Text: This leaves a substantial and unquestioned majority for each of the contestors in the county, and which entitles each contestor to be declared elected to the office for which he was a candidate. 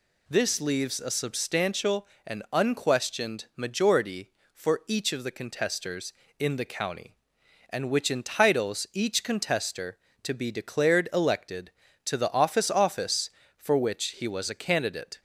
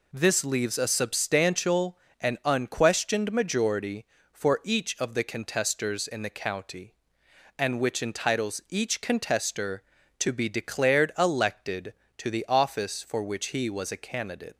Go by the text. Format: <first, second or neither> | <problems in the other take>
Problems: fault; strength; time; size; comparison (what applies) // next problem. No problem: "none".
second | says "office" twice; at 12.6 s